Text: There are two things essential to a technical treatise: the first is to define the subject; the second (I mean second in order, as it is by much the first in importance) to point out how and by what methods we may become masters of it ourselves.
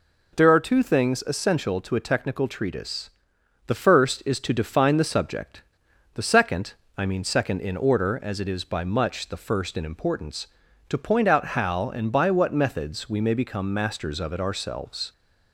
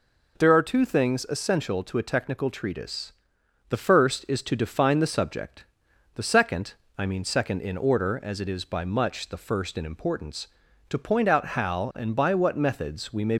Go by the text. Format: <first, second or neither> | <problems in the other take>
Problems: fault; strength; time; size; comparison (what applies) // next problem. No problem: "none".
first | stops before "become masters of it ourselves"; at 13.3 s